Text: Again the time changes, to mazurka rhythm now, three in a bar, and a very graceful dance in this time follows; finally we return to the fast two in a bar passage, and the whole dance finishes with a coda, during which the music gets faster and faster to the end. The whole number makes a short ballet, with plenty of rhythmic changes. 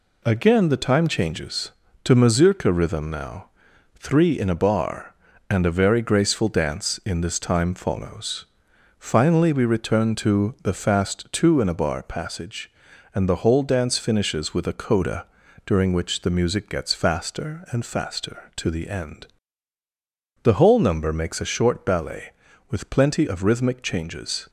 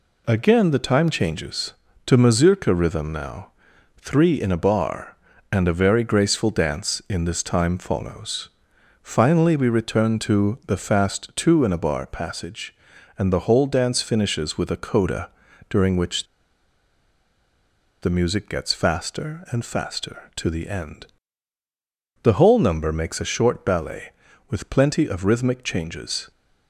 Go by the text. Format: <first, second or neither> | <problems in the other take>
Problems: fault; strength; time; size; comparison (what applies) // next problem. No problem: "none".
first | pauses between "which" and "the"; strong; at 16.2 s; 1.7 s long